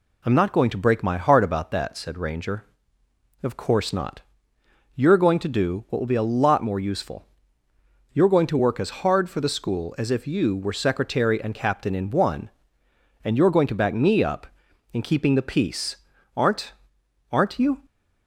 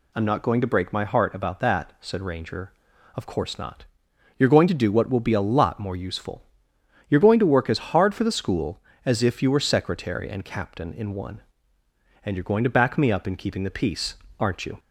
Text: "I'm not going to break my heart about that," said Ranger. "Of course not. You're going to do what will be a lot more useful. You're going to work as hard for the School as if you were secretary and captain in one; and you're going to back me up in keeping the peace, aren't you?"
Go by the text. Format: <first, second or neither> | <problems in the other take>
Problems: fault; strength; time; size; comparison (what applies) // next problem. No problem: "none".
second | says "aren't" twice; at 17.3 s